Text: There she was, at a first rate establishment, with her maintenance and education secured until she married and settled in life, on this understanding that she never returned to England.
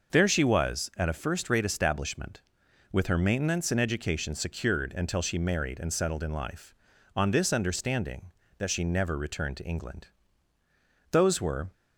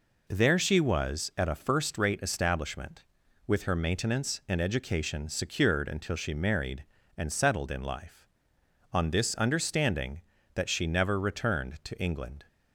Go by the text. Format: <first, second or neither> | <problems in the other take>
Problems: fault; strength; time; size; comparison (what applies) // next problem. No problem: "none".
second | goes on to say "Those were"; from 11.1 s on; 0.58 s long